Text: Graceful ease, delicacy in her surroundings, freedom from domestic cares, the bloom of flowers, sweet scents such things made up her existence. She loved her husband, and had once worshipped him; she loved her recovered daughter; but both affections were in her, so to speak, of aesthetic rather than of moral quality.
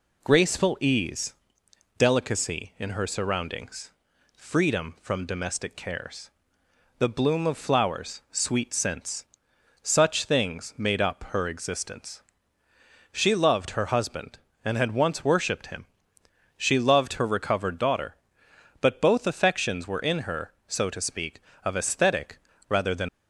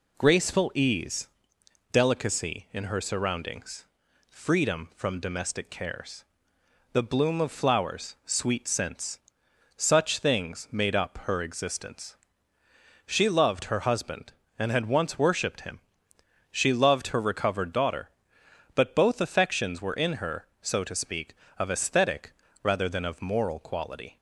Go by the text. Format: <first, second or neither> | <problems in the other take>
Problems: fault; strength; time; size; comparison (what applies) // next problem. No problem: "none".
second | pauses between "scents" and "such"; noticeable; at 9.2 s; 0.56 s long; noticeable in the second // pauses between "aesthetic" and "rather"; slight; at 22.3 s; 0.32 s long; slight in the second // stops before "of moral quality"; at 23.0 s